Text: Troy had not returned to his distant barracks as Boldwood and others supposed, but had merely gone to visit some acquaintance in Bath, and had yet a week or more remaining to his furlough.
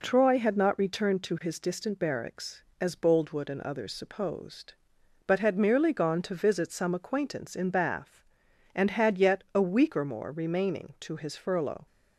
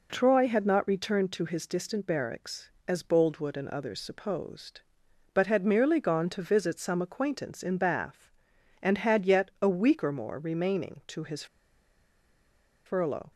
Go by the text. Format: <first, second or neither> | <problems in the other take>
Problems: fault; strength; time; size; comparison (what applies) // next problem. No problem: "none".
first | pauses between "his" and "furlough"; strong; at 11.4 s; 1.4 s long